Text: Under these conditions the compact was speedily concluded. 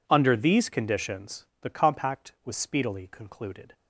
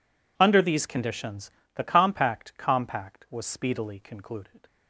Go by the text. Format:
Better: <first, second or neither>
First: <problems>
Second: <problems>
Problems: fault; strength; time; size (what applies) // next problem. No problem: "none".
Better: first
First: none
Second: pauses between "conditions" and "the"; slight; at 1.4 s; 0.26 s long // says "compact" twice; at 2.5 s